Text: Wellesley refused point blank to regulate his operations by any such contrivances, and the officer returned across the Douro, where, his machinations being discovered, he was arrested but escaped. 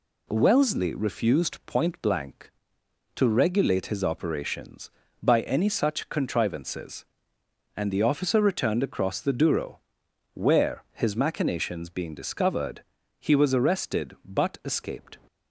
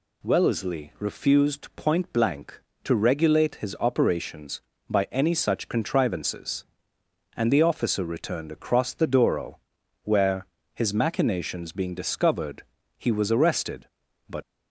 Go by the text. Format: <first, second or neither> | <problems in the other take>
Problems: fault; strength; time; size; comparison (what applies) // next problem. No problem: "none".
first | stops before "escaped"; at 14.4 s